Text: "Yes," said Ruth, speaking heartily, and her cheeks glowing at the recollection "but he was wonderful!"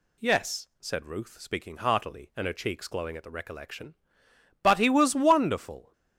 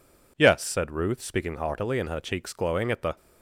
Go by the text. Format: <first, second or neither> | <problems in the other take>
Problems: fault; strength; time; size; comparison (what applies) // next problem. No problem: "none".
first | stops before "recollection but he was wonderful"; at 3.1 s